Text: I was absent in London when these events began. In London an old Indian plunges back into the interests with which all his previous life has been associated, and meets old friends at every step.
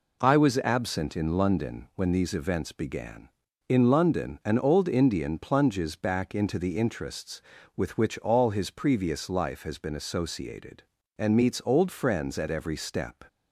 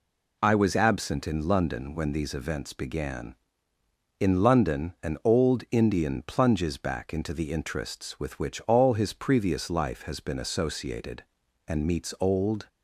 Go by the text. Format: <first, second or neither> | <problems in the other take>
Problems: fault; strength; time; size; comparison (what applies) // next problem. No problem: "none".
first | stops before "friends at every step"; at 12.6 s